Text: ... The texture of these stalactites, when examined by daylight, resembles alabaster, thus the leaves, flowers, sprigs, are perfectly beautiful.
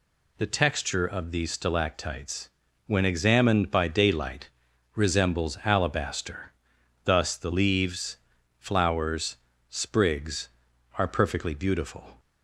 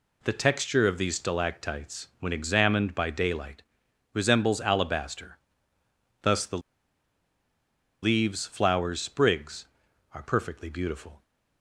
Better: first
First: none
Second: pauses between "the" and "leaves"; strong; at 6.5 s; 1.4 s long

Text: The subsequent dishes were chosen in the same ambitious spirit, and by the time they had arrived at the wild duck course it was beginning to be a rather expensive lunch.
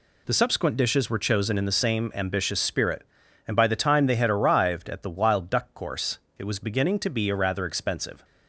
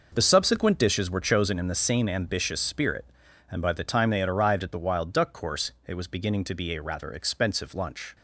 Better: second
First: pauses between "course" and "it"; slight; at 6.1 s; 0.18 s long // stops before "lunch"; at 8.2 s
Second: pauses between "course" and "it"; slight; at 5.7 s; 0.16 s long

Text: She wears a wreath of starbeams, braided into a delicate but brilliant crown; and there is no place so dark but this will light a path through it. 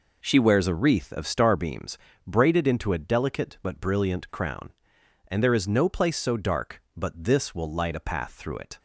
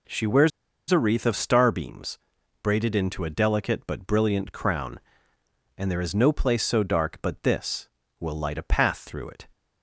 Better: first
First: none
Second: pauses between "wears" and "a"; at 0.5 s; 0.40 s long

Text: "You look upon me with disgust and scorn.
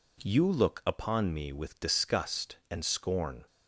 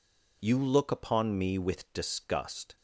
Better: first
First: none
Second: stops before "and scorn"; at 2.7 s

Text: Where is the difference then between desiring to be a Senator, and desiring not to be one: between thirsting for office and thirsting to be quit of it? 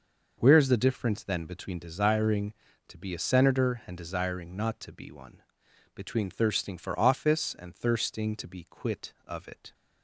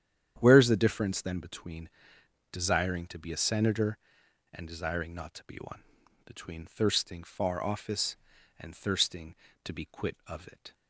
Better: first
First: none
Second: starts louder than the rest; strong; until 1.3 s; 9.5 dB // pauses between "between" and "desiring"; noticeable; at 1.8 s; 0.62 s long // says "far" for "for"; at 7.2 s

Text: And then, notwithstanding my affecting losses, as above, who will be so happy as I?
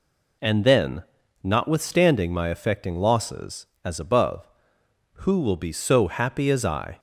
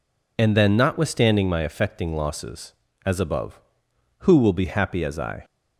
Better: first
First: none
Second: skips "so"; at 4.6 s

